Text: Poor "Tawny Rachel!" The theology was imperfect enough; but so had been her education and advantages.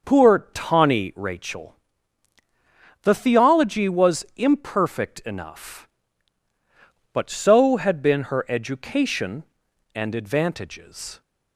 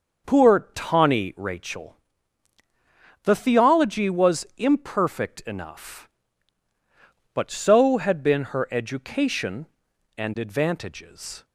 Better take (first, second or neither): neither